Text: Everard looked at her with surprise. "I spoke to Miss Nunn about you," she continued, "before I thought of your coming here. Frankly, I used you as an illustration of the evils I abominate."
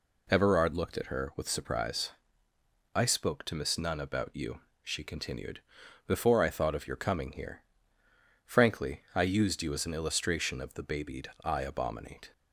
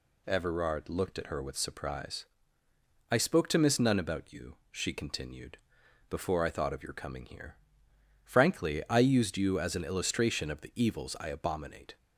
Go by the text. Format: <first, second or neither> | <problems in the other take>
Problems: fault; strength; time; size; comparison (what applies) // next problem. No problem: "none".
second | says "babied" for "evils"; at 10.8 s